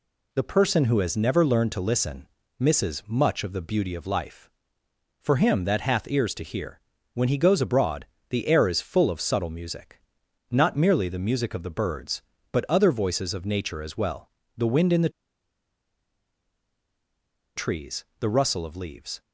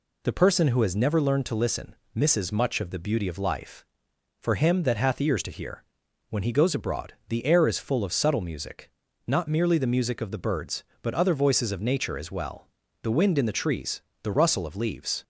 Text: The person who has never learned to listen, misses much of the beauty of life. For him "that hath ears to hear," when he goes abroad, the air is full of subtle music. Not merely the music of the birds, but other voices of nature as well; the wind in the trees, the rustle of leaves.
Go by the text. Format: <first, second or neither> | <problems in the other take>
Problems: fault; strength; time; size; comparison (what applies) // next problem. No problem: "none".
second | pauses between "the" and "trees"; strong; at 15.0 s; 2.4 s long